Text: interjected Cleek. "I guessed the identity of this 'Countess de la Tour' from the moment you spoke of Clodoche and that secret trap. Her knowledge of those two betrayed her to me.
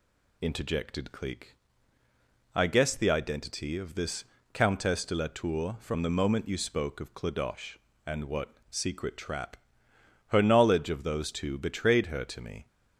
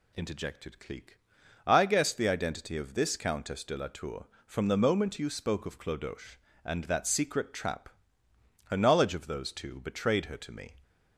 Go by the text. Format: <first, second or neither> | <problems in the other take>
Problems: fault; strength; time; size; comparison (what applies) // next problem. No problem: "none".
second | pauses between "this" and "Countess"; slight; at 4.2 s; 0.28 s long // says "what" for "that"; at 8.2 s